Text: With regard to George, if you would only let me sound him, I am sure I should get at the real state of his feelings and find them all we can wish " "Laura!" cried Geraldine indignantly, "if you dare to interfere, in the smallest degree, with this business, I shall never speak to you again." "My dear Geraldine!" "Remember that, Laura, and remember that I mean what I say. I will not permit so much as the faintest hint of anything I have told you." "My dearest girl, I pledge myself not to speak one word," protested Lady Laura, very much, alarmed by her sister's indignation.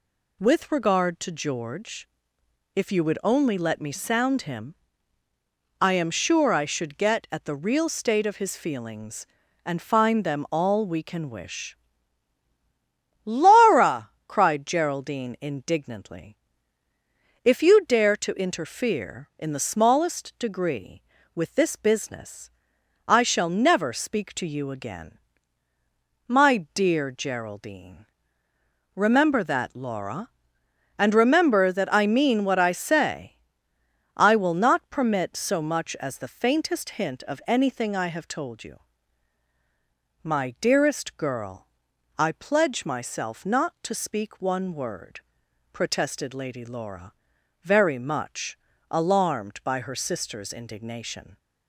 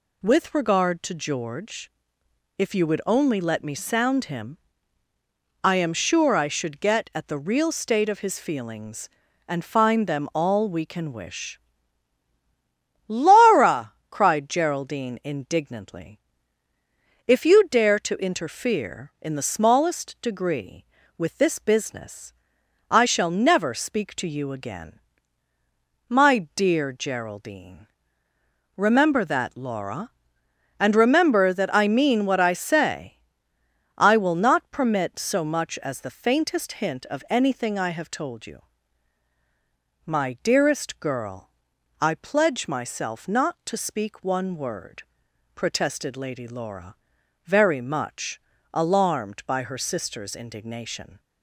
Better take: neither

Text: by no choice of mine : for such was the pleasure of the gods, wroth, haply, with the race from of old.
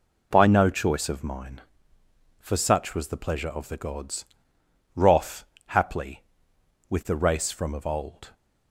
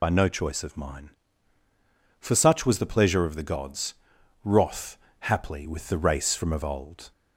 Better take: first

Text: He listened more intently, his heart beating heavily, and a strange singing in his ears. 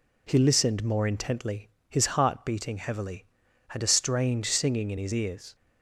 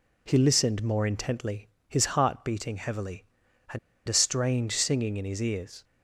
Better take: first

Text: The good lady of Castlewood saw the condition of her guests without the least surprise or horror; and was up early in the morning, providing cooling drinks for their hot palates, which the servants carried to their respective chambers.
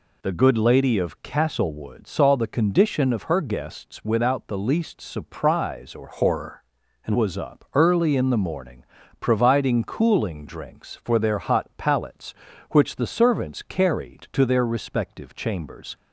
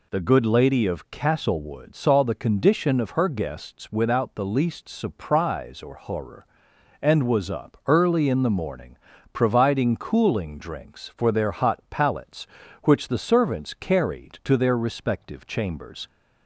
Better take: second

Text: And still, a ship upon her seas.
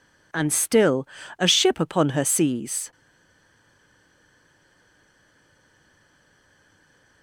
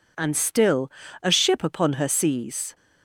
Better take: second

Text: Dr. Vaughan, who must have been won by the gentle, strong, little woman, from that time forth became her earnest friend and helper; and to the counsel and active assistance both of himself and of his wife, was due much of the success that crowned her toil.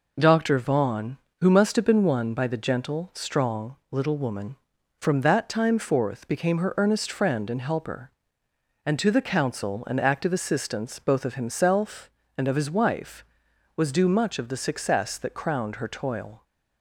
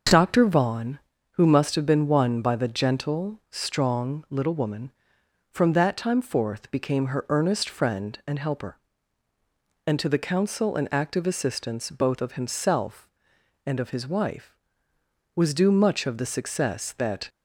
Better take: first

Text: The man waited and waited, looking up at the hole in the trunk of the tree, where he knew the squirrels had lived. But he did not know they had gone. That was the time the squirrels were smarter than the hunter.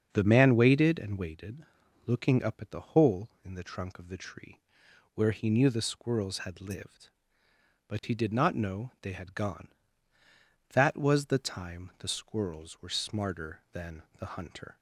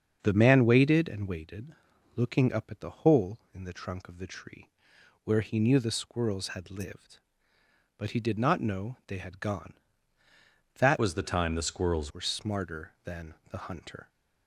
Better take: first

